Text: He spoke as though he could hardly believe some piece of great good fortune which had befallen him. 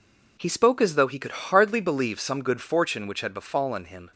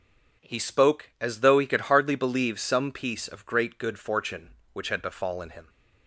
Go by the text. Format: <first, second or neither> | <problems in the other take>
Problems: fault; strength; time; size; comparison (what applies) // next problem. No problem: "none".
second | skips "piece of great"; at 2.4 s